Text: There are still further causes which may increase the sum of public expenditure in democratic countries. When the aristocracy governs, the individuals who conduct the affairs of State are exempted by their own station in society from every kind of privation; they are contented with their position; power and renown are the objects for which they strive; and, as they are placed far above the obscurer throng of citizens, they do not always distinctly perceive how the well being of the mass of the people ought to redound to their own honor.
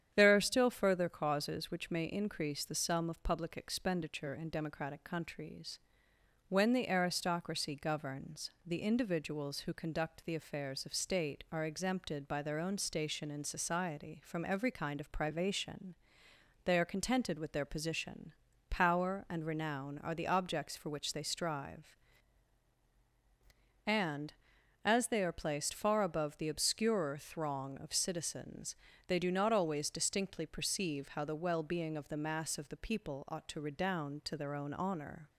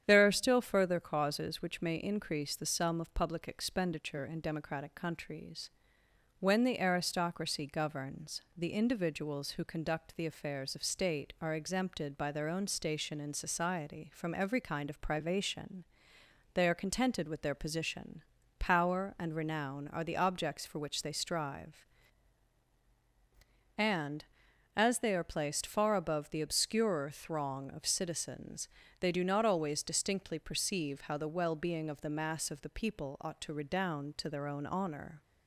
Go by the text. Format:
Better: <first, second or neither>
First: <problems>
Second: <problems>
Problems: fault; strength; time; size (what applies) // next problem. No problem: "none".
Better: neither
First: starts louder than the rest; strong; until 1.1 s; 9 dB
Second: starts louder than the rest; strong; until 1.0 s; 9 dB